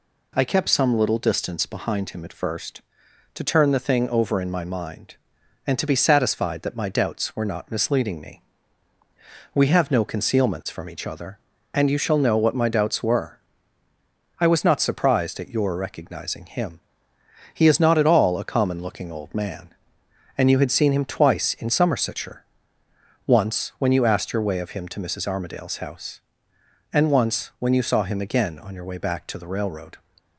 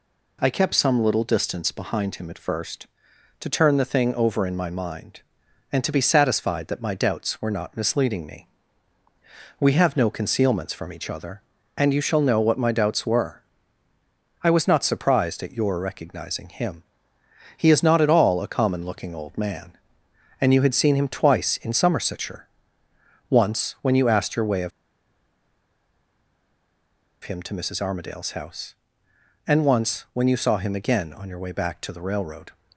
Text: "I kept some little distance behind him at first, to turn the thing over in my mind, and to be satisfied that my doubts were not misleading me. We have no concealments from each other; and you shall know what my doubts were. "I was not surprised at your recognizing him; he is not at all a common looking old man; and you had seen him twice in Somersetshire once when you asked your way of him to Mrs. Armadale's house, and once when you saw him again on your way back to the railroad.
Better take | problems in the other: first | pauses between "Somersetshire" and "once"; noticeable; at 22.4 s; 0.82 s long; noticeable in the first // pauses between "of" and "him"; strong; at 24.7 s; 2.5 s long

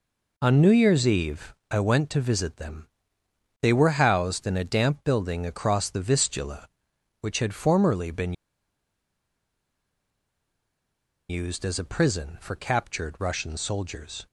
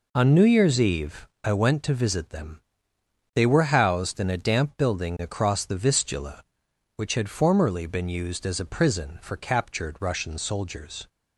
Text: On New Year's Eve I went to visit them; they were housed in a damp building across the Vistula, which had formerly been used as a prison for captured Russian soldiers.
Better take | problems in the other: second | pauses between "Eve" and "I"; slight; at 1.5 s; 0.16 s long; slight in the second // pauses between "been" and "used"; strong; at 8.3 s; 2.9 s long

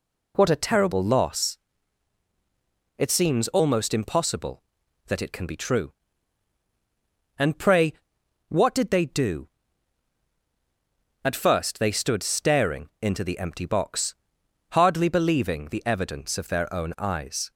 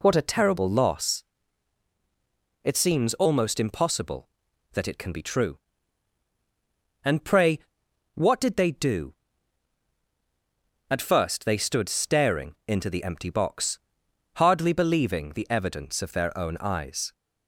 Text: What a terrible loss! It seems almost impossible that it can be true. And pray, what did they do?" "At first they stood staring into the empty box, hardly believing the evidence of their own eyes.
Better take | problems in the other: neither | none

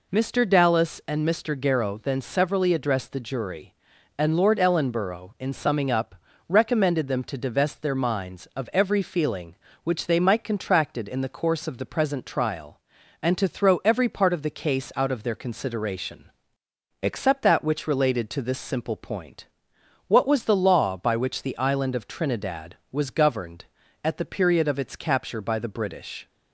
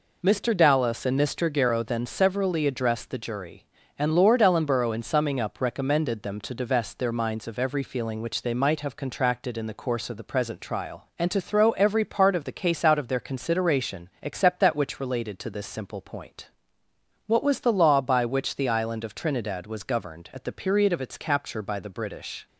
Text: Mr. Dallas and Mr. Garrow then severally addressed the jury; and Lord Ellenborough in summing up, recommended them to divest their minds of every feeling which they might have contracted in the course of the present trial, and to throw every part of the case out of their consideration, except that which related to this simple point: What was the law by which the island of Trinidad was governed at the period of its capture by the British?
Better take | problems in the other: second | skips "have"; at 10.4 s

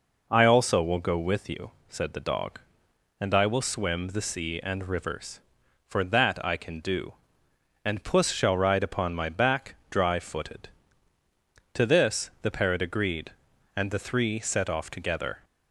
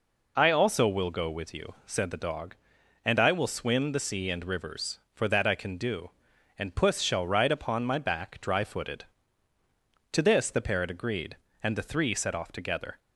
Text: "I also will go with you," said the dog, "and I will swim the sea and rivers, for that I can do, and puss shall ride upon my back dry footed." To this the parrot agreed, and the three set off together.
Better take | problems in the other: first | loses the start of "I"; at 0.3 s; 35 ms

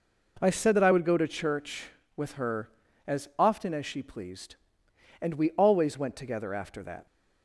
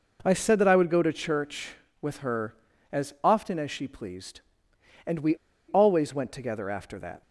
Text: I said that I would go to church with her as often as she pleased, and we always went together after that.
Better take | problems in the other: first | pauses between "we" and "always"; slight; at 5.3 s; 0.33 s long

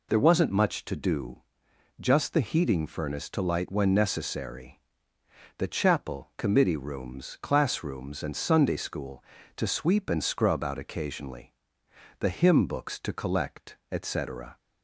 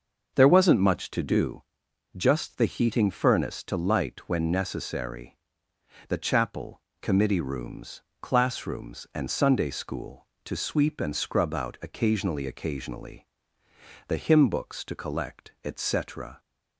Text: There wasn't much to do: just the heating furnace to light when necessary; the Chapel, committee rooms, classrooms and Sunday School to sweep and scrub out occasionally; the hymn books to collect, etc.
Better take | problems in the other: first | starts louder than the rest; until 1.3 s; 6 dB // says "occasionally" twice; at 12.4 s

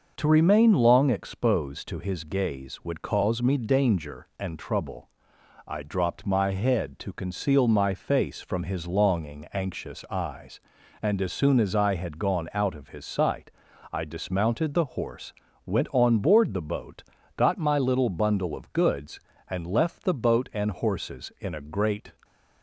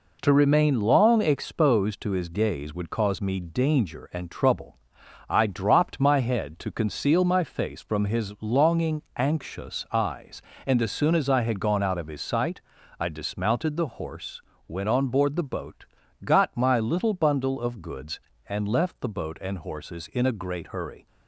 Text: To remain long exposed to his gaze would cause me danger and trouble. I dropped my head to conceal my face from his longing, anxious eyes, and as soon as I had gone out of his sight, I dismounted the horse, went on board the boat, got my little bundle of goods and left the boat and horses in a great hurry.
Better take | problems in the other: second | starts louder than the rest; noticeable; until 1.2 s; 6 dB // stops before "hurry"; at 22.2 s

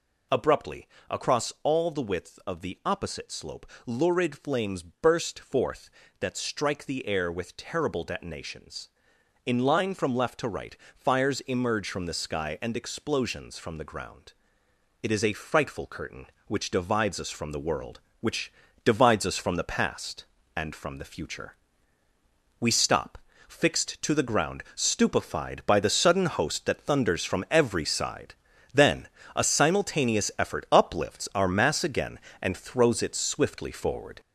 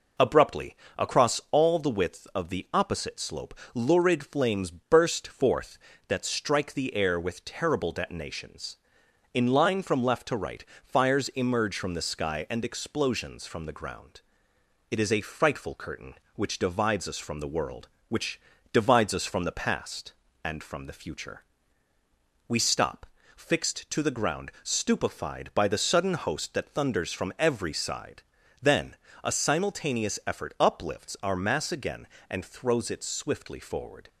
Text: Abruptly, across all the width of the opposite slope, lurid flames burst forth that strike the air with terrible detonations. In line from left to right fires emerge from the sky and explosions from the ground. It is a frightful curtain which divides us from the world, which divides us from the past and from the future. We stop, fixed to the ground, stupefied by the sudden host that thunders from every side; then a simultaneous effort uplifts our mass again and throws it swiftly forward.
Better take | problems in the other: second | gets louder; noticeable; throughout; 6 dB // pauses between "right" and "fires"; slight; at 10.7 s; 0.20 s long; slight in the second // pauses between "which" and "divides"; slight; at 18.5 s; 0.32 s long; slight in the second // pauses between "then" and "a"; slight; at 29.0 s; 0.26 s long; slight in the second

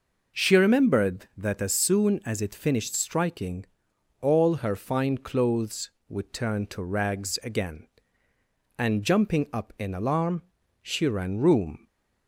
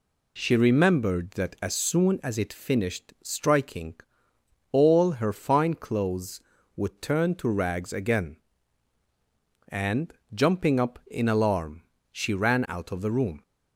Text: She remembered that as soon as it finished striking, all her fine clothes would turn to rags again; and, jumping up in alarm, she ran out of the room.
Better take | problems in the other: second | skips "out of the"; at 11.3 s // stays silent after the last word; slight; from 11.7 s on; 0.5 s long

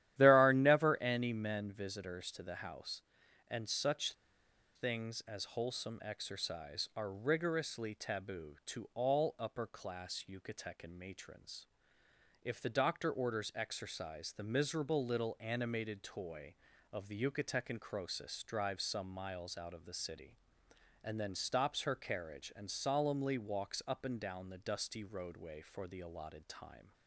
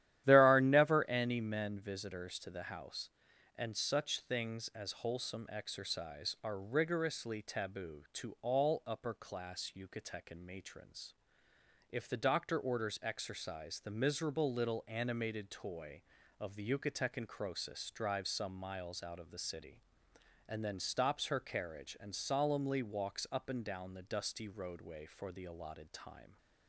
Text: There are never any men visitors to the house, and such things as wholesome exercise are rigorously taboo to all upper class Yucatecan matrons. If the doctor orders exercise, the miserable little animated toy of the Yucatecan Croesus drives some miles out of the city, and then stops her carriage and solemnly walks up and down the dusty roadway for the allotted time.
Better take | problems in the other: second | starts louder than the rest; strong; until 1.1 s; 12 dB; strong in the second // pauses between "such" and "things"; noticeable; at 4.1 s; 0.63 s long

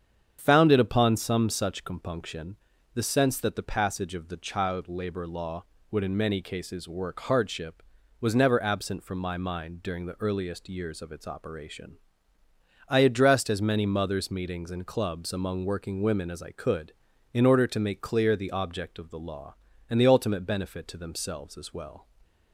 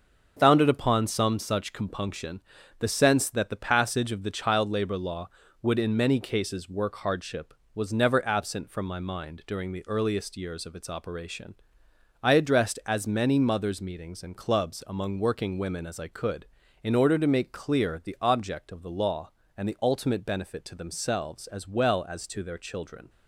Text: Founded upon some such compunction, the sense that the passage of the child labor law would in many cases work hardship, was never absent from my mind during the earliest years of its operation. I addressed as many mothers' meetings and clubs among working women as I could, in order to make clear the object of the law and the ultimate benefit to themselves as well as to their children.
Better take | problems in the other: second | starts louder than the rest; strong; until 1.4 s; 8 dB; also in the second // stops before "as to their children"; at 22.2 s

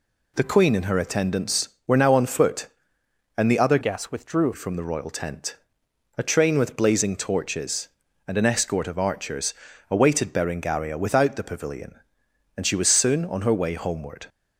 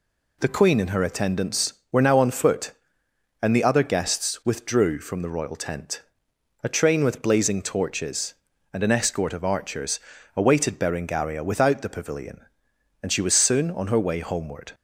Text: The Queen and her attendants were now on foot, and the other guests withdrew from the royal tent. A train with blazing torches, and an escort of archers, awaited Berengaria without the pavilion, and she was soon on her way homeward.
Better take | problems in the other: second | changes voice from "guests" to "withdrew"; from 3.8 to 4.5 s; 0.7 s long

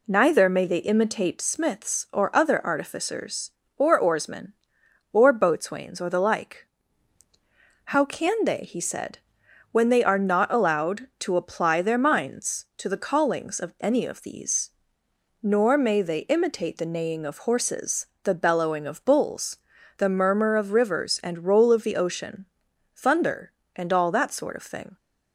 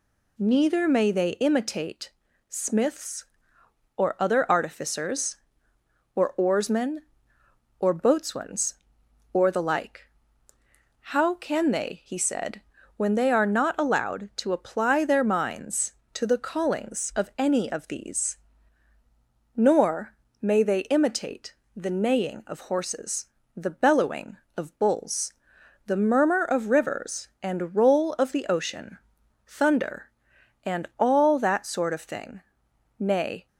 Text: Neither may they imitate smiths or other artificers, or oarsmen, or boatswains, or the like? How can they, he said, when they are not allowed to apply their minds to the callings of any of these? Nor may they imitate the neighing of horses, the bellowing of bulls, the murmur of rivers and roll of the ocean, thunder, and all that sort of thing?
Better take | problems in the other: first | pauses between "imitate" and "smiths"; slight; at 2.1 s; 0.36 s long // pauses between "Nor" and "may"; slight; at 20.1 s; 0.24 s long // pauses between "imitate" and "the"; slight; at 21.5 s; 0.22 s long // goes on to say "Nay"; slight; from 32.9 s on; 0.48 s long

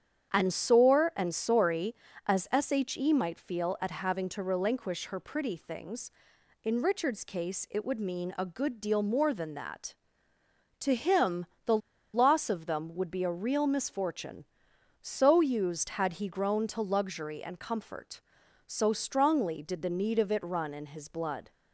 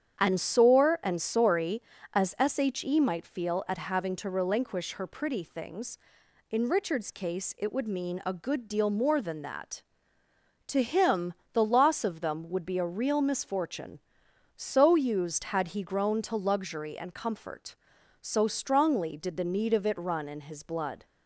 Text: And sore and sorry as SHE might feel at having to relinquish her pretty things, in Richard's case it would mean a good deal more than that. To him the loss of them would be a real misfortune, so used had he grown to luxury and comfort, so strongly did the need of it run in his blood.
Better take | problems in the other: second | starts louder than the rest; strong; until 1.3 s; 8.5 dB; strong in the second // pauses between "him" and "the"; slight; at 11.4 s; 0.20 s long; slight in the second // pauses between "the" and "loss"; at 11.7 s; 0.36 s long

